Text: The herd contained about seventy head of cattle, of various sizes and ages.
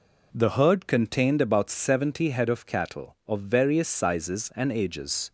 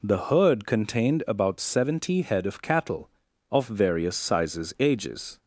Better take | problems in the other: first | skips "and"; at 4.7 s

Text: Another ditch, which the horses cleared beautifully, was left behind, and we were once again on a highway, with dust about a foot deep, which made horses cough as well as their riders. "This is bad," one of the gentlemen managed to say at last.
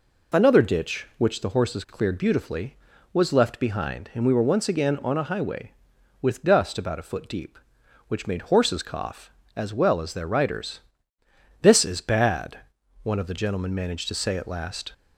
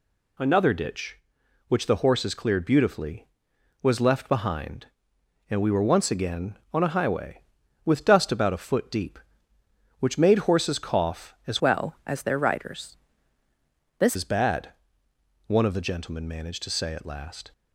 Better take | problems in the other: first | changes voice from "well" to "This"; from 11.6 to 14.1 s; 2.5 s long

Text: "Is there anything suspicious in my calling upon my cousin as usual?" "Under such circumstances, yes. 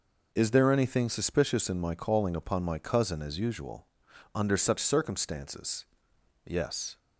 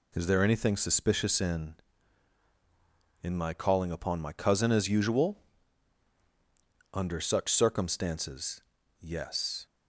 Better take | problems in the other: first | says "in" twice; at 3.2 s

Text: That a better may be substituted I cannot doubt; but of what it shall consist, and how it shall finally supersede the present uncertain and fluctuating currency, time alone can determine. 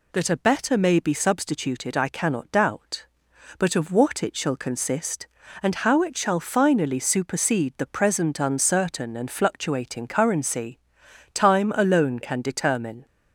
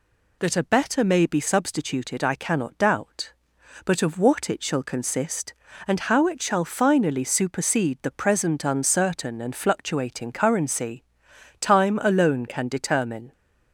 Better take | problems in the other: neither | none

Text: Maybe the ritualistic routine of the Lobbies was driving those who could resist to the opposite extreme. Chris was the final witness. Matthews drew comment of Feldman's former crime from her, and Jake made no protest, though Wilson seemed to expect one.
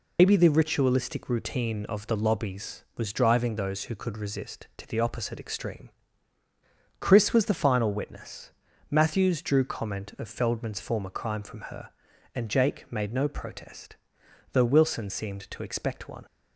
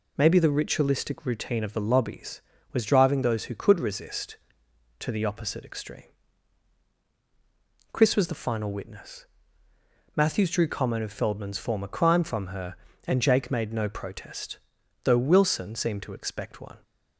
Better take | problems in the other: second | loses the start of "Maybe"; at 0.1 s; 135 ms

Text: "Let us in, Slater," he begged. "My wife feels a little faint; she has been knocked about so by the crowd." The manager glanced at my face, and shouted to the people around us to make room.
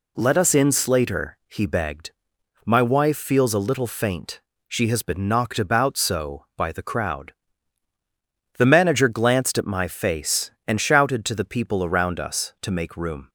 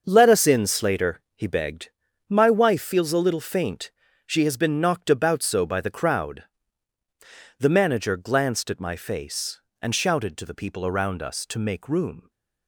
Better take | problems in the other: first | gets quieter; strong; throughout; 9.5 dB

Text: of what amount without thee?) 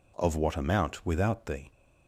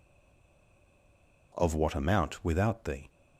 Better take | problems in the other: first | stays silent before the first word; noticeable; until 1.5 s; 1.5 s long

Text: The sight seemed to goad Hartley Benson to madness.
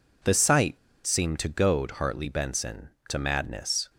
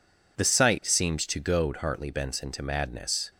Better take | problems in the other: second | pauses between "sight" and "seemed"; slight; at 0.7 s; 0.27 s long

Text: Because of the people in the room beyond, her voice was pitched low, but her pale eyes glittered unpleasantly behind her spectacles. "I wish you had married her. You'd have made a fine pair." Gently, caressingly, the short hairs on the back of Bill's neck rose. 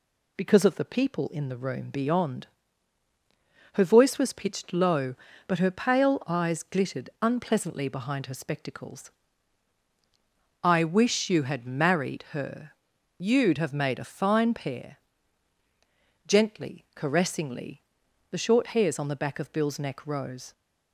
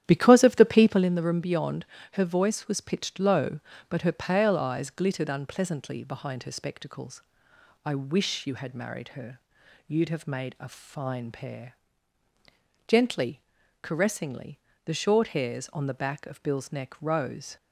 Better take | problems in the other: first | starts louder than the rest; strong; until 1.1 s; 11 dB

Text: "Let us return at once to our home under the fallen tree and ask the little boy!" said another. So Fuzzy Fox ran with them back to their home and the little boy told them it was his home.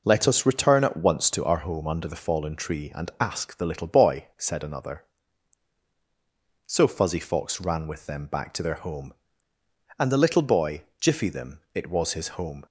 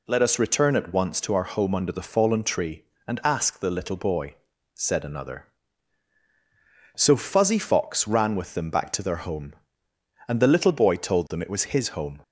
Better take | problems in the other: second | says "jiffy" for "told"; at 10.9 s

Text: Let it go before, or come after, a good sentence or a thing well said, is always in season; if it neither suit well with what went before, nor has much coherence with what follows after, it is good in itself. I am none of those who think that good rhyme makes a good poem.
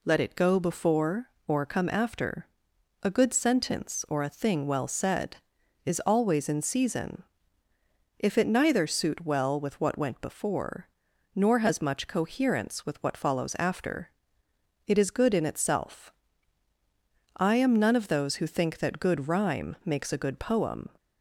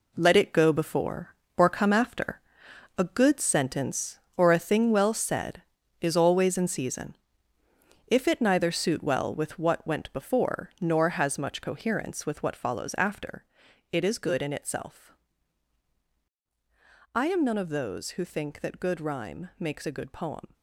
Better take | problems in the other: first | gets quieter; strong; throughout; 8 dB

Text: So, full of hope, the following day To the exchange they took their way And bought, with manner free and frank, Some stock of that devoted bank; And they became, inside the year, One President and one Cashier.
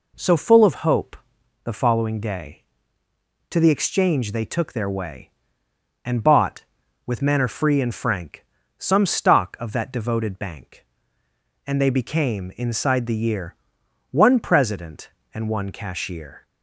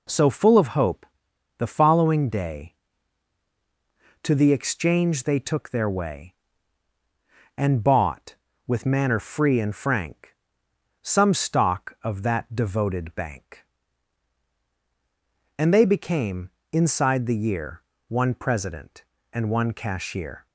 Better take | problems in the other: neither | none

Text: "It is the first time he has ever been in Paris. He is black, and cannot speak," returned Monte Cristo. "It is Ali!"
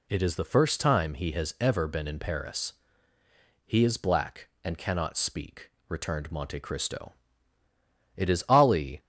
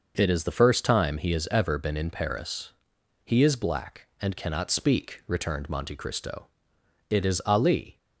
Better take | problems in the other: neither | none

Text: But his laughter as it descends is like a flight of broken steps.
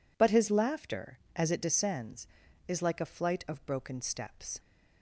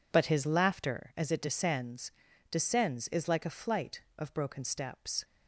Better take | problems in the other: first | says "descends" twice; at 2.5 s

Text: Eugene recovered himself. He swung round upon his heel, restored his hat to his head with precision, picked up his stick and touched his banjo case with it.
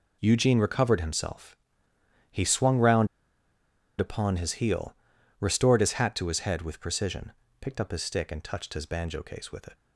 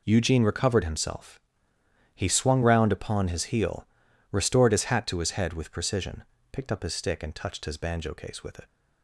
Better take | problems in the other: second | pauses between "round" and "upon"; noticeable; at 3.0 s; 0.92 s long

